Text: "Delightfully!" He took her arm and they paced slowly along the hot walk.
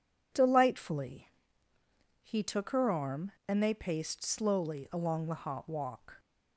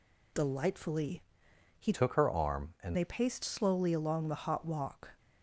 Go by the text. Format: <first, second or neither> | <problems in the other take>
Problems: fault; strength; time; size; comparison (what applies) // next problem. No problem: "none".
first | changes voice from "took" to "and"; from 1.9 to 2.9 s; 1.0 s long